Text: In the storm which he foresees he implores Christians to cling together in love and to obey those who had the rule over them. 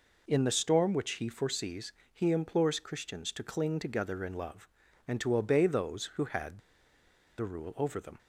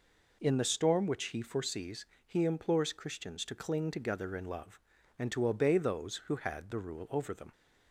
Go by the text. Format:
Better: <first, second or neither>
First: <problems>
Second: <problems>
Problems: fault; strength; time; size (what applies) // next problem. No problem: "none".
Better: second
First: pauses between "foresees" and "he"; slight; at 1.9 s; 0.22 s long // pauses between "had" and "the"; noticeable; at 6.6 s; 0.77 s long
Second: pauses between "foresees" and "he"; slight; at 2.0 s; 0.22 s long